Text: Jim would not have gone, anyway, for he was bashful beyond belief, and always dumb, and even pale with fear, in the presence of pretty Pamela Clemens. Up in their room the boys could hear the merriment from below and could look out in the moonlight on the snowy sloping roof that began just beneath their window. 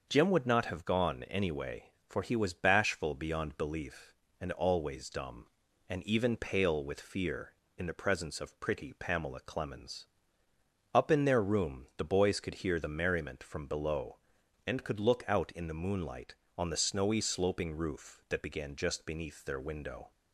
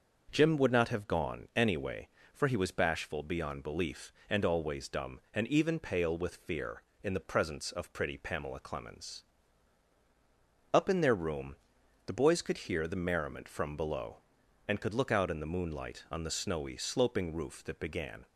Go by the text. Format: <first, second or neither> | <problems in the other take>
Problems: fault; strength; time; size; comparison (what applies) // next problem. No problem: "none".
first | starts louder than the rest; until 1.3 s; 6 dB; noticeable in the first // pauses between "room" and "the"; noticeable; at 11.5 s; 0.50 s long // stops before "just beneath their window"; at 18.2 s